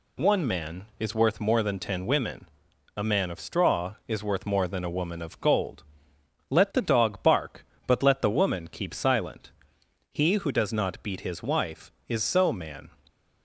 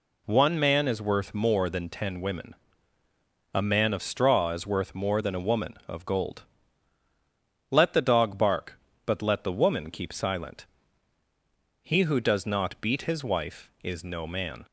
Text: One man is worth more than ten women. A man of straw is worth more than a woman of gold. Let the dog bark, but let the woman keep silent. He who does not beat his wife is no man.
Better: second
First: says "so" for "no"; at 12.2 s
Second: none

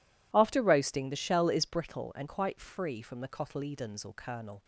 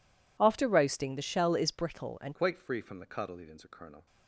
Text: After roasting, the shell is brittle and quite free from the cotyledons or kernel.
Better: first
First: none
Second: changes voice at "quite"; from 2.3 s on; 1.7 s long

